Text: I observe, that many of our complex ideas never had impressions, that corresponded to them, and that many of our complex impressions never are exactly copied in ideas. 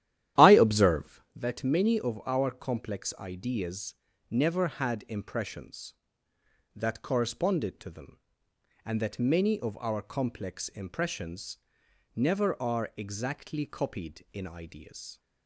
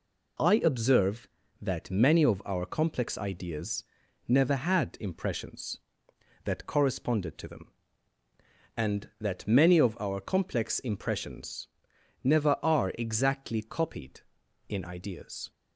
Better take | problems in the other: second | starts louder than the rest; strong; until 1.3 s; 12 dB // pauses between "ideas" and "never"; at 3.9 s; 0.38 s long; noticeable in the second // pauses between "impressions" and "never"; noticeable; at 11.5 s; 0.58 s long; noticeable in the second

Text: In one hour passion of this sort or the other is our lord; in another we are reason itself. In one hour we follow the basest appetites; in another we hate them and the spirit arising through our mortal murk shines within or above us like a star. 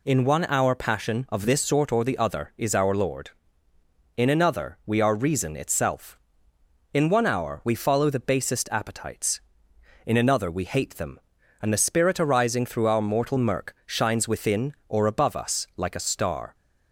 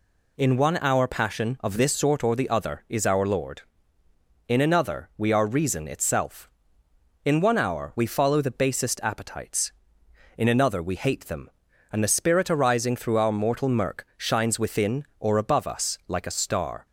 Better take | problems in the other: neither | none

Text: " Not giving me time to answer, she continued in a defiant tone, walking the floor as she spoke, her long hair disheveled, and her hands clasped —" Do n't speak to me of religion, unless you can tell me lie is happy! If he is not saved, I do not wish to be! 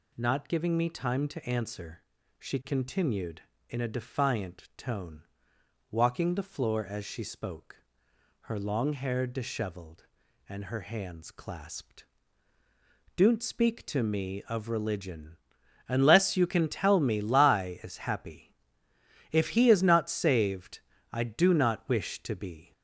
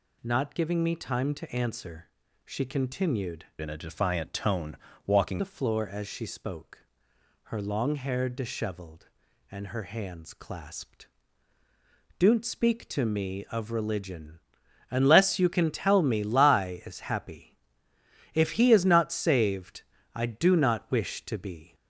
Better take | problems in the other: first | changes voice from "in" to "walking"; from 3.6 to 5.4 s; 1.8 s long

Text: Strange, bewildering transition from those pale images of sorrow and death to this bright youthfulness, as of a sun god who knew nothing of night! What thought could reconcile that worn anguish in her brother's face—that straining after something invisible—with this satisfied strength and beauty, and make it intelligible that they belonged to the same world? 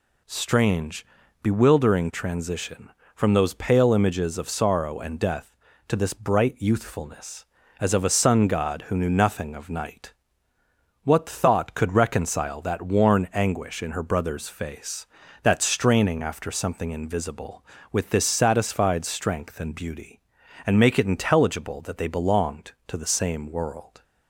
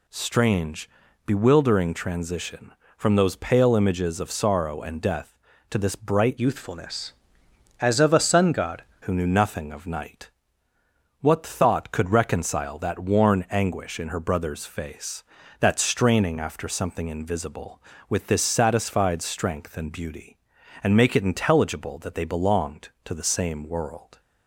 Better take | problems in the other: first | changes voice from "youthfulness" to "god"; from 6.3 to 8.8 s; 2.5 s long

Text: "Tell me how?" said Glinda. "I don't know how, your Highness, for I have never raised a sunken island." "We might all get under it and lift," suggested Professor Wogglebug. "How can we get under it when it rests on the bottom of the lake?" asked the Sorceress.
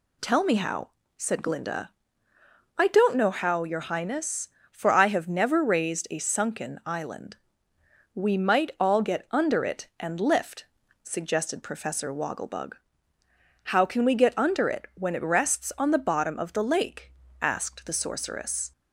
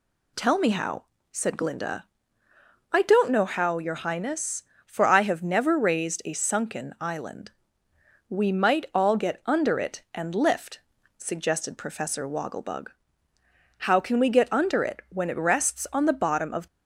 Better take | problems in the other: first | stops before "the lake asked the Sorceress"; at 16.6 s

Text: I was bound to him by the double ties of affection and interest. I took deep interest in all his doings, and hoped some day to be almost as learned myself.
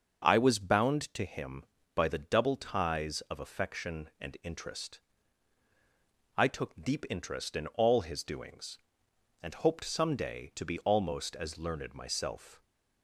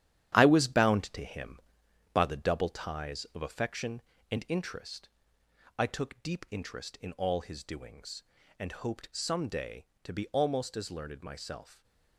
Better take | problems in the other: first | gets quieter; strong; throughout; 8.5 dB // starts louder than the rest; strong; until 1.4 s; 11 dB; also in the first

